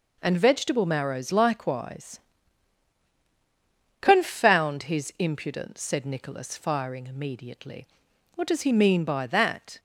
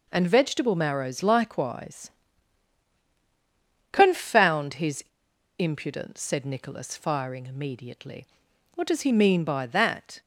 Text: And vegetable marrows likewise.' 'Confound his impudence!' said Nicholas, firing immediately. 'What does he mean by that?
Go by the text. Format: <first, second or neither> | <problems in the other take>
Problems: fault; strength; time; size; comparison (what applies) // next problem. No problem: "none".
first | pauses between "his" and "impudence"; noticeable; at 5.0 s; 0.54 s long